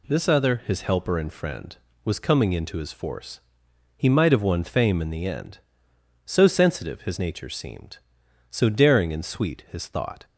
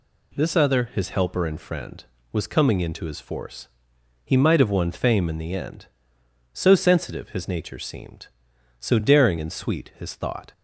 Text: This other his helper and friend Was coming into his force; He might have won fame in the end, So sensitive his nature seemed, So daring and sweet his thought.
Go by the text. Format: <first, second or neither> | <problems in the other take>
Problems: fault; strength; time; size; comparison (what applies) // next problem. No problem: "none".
neither | none